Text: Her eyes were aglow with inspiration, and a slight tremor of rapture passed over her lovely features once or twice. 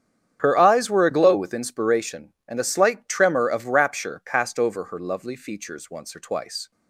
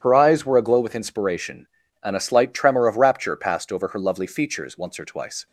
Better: neither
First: starts louder than the rest; strong; until 1.4 s; 9 dB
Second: starts louder than the rest; strong; until 1.0 s; 9.5 dB

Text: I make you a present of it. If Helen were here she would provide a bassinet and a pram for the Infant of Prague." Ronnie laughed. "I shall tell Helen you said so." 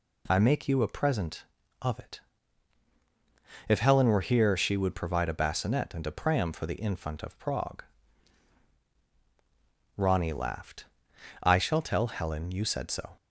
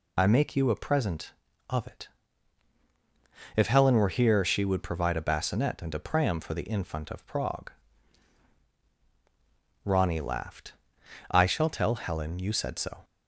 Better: first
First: none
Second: loses the start of "I"; at 0.1 s; 40 ms

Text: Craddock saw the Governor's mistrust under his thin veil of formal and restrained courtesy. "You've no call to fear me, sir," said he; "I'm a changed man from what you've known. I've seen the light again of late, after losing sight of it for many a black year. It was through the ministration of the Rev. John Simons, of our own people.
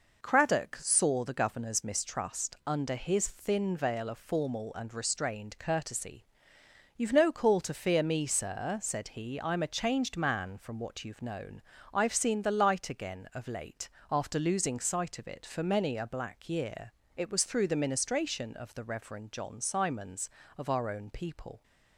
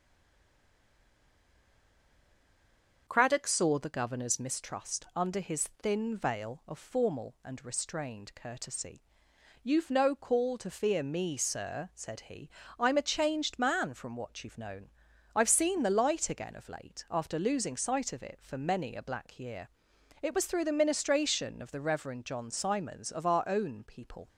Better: first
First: none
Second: stays silent before the first word; strong; until 3.0 s; 3.0 s long // starts louder than the rest; until 4.0 s; 6.5 dB

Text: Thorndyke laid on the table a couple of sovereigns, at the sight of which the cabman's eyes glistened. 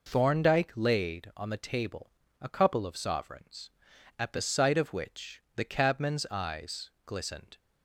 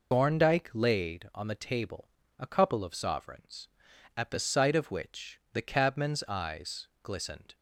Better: first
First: pauses between "table" and "a"; slight; at 2.1 s; 0.28 s long // pauses between "eyes" and "glistened"; slight; at 6.9 s; 0.16 s long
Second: loses the start of "Thorndyke"; at 0.1 s; 90 ms // pauses between "table" and "a"; slight; at 2.0 s; 0.28 s long // pauses between "eyes" and "glistened"; slight; at 6.8 s; 0.16 s long

